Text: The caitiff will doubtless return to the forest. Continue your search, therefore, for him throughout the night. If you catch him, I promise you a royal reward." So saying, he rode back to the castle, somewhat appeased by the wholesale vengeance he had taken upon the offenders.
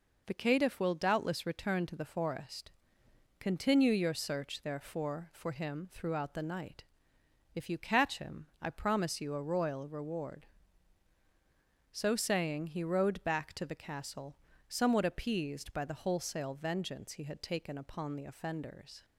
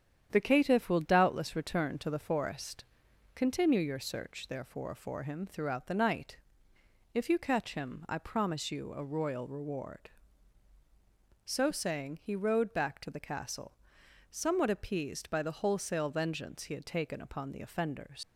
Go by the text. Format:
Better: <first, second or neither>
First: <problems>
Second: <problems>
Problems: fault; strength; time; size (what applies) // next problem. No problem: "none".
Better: first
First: none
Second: starts louder than the rest; strong; until 1.3 s; 9 dB // leaves "offenders" unfinished; at 18.2 s; 100 ms